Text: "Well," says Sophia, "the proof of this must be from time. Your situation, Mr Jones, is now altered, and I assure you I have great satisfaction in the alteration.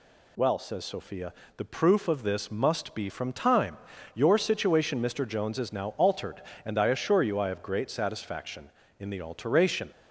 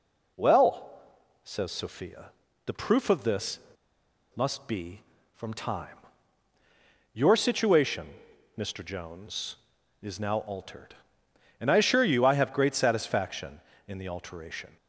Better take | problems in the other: first | pauses between "this" and "must"; noticeable; at 3.5 s; 0.77 s long

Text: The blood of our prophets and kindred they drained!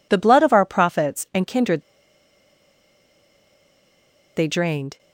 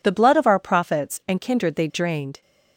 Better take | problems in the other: second | pauses between "kindred" and "they"; strong; at 1.8 s; 2.5 s long

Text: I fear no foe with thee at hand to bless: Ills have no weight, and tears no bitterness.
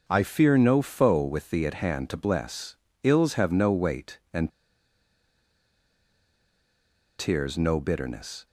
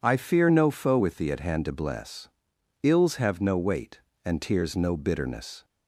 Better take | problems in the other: second | pauses between "and" and "tears"; strong; at 4.5 s; 2.6 s long

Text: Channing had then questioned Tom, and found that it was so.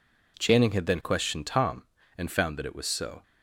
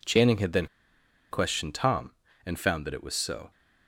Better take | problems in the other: first | pauses between "then" and "questioned"; noticeable; at 0.6 s; 0.65 s long

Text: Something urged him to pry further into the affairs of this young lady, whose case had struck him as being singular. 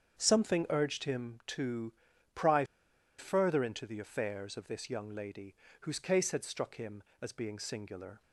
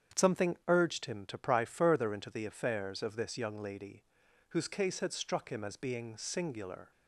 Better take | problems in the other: second | starts louder than the rest; strong; until 1.2 s; 7.5 dB; strong in the second // pauses between "to" and "pry"; at 1.9 s; 0.42 s long // pauses between "pry" and "further"; noticeable; at 2.6 s; 0.54 s long

